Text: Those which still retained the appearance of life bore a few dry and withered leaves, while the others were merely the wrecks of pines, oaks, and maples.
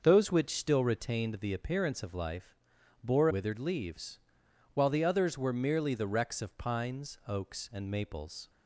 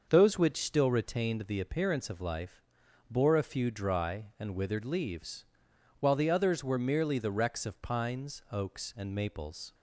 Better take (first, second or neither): second